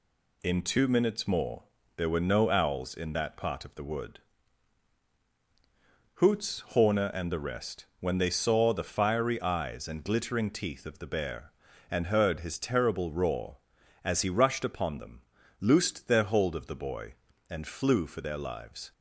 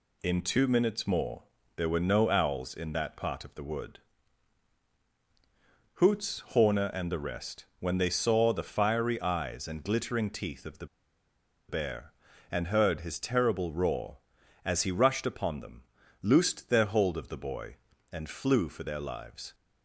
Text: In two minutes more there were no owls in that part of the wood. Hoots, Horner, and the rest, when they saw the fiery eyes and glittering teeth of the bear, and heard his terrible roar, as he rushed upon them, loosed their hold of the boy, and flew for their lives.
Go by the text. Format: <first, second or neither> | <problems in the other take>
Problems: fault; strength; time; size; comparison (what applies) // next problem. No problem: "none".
first | pauses between "more" and "there"; slight; at 1.4 s; 0.34 s long; slight in the first // pauses between "the" and "bear"; noticeable; at 10.8 s; 0.83 s long